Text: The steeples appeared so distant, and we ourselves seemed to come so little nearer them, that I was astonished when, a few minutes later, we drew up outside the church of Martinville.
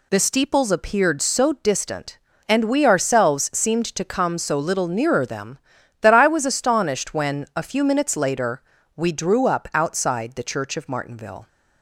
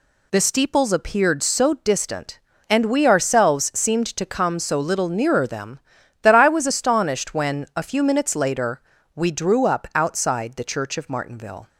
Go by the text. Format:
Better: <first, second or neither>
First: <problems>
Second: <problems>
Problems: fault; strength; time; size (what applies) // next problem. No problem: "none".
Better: neither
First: none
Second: none